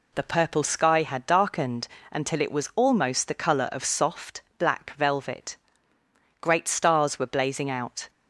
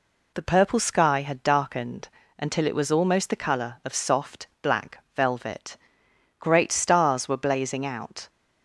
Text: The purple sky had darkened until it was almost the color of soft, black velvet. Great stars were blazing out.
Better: neither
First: pauses between "darkened" and "until"; slight; at 1.8 s; 0.24 s long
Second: pauses between "darkened" and "until"; slight; at 2.0 s; 0.30 s long

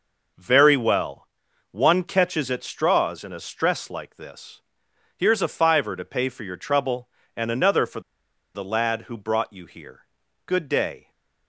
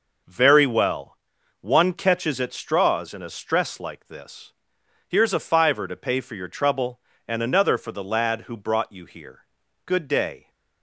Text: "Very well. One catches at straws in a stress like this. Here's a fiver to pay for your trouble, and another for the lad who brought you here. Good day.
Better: second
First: pauses between "for" and "the"; noticeable; at 7.9 s; 0.54 s long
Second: none

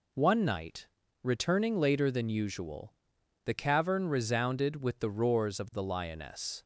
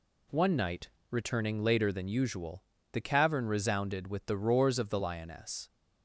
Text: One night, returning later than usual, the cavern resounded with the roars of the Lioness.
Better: neither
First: none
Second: none

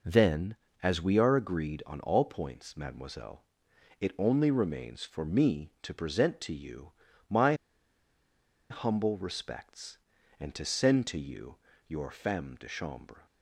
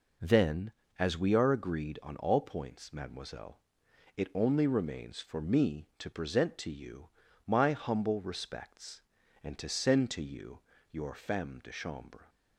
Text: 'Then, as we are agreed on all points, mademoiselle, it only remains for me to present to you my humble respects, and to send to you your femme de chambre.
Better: second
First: pauses between "you" and "my"; at 6.9 s; 0.38 s long // pauses between "my" and "humble"; at 7.5 s; 1.1 s long // pauses between "you" and "your"; slight; at 11.5 s; 0.32 s long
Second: pauses between "you" and "my"; at 7.0 s; 0.38 s long // pauses between "you" and "your"; slight; at 10.5 s; 0.32 s long

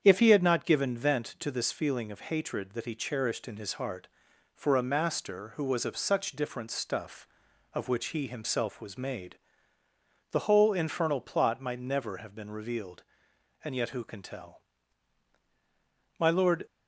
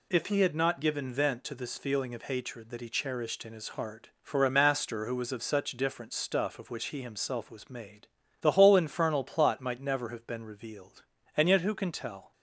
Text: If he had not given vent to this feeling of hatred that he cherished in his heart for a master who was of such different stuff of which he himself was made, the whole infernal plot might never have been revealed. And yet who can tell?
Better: second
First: starts louder than the rest; strong; until 1.0 s; 8 dB // goes on to say "My lord"; slight; from 16.1 s on; 0.48 s long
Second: none

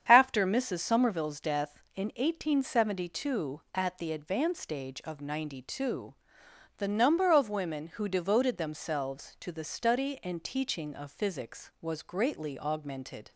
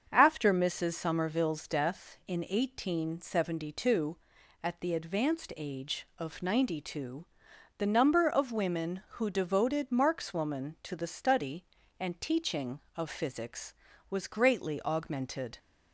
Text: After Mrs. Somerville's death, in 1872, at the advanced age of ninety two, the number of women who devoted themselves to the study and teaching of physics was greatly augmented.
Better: first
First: starts louder than the rest; strong; until 1.0 s; 8 dB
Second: starts louder than the rest; until 1.1 s; 7 dB // says "markswoman" for "themselves"; at 9.8 s

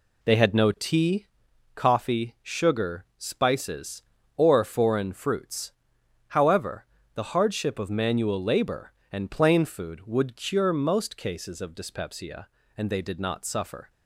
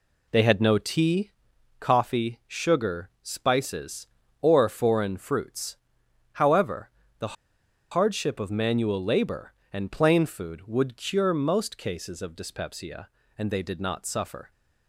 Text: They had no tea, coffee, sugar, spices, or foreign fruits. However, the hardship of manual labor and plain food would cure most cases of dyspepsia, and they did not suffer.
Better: first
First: none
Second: pauses between "the" and "hardship"; noticeable; at 7.3 s; 0.57 s long

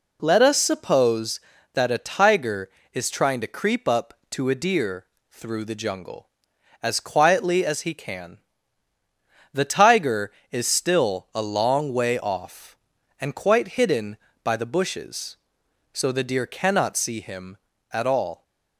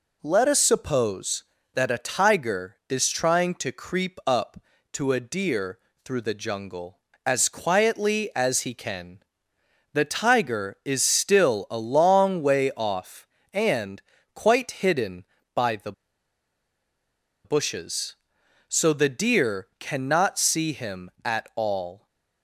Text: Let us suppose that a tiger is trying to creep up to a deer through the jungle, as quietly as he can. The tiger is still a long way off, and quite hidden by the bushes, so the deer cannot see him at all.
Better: first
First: pauses between "deer" and "through"; slight; at 5.0 s; 0.24 s long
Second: pauses between "deer" and "through"; slight; at 5.7 s; 0.26 s long // pauses between "and" and "quite"; slight; at 14.0 s; 0.32 s long // pauses between "the" and "bushes"; strong; at 15.9 s; 1.5 s long

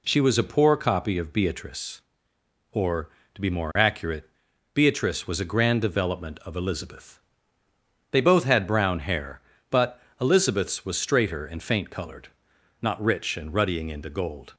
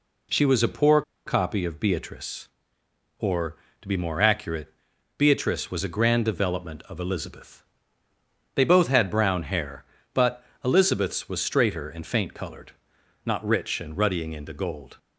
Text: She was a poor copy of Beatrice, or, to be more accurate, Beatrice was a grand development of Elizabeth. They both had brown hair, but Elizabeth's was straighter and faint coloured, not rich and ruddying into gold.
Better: first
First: pauses between "but" and "Elizabeth's"; slight; at 10.0 s; 0.18 s long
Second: pauses between "poor" and "copy"; slight; at 1.0 s; 0.24 s long // pauses between "but" and "Elizabeth's"; slight; at 10.4 s; 0.18 s long

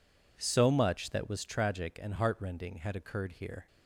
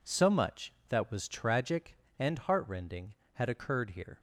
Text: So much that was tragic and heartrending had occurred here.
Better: neither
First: none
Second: none

